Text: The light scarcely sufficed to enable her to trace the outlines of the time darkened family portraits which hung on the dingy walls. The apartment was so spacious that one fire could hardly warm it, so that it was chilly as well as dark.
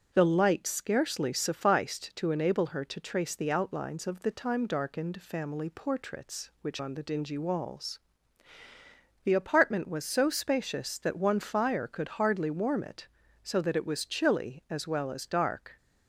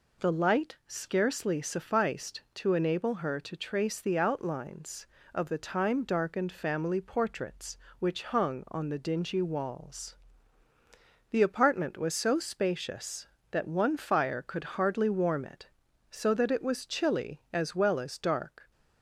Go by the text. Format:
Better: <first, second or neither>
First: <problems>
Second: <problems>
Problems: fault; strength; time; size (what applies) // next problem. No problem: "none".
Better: second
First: starts louder than the rest; strong; until 1.1 s; 7.5 dB // skips "hung"; at 6.7 s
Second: none